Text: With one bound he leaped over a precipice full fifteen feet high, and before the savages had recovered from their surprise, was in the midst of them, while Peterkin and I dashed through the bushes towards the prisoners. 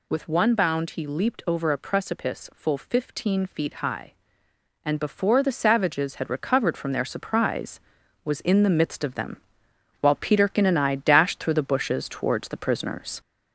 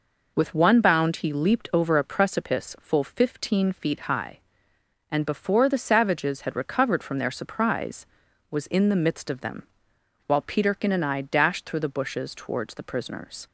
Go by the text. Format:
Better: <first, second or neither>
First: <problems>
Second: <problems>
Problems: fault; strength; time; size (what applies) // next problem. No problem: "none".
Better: second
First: gets louder; slight; throughout; 3 dB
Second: none